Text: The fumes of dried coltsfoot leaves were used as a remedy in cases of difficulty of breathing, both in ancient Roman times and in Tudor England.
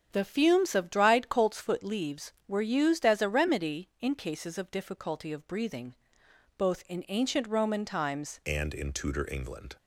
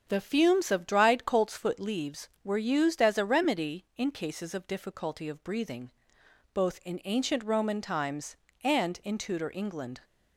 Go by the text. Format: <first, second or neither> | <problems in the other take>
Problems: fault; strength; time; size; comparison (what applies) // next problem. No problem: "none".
second | starts louder than the rest; strong; until 1.1 s; 8 dB; strong in the second // changes voice at "and"; from 8.4 s on; 1.3 s long